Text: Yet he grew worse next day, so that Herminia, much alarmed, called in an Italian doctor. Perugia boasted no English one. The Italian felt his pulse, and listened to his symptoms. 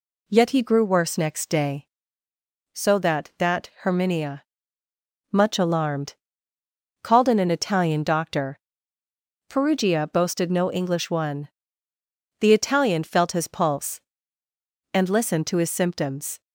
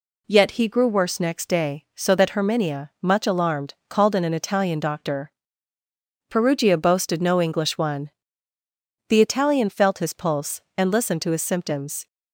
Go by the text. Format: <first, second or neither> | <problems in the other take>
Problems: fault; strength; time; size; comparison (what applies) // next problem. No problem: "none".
second | says "that" twice; at 3.3 s